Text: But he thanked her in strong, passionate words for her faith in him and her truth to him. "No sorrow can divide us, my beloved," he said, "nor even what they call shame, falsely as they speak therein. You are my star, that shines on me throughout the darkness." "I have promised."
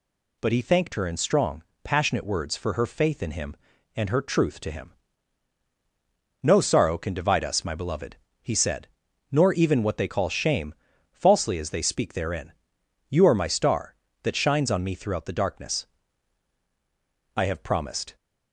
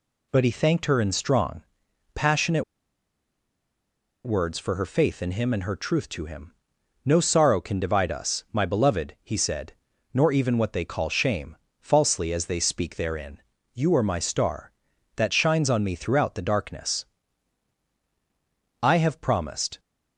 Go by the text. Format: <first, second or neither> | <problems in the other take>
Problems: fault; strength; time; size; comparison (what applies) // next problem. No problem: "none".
first | pauses between "passionate" and "words"; strong; at 2.6 s; 1.6 s long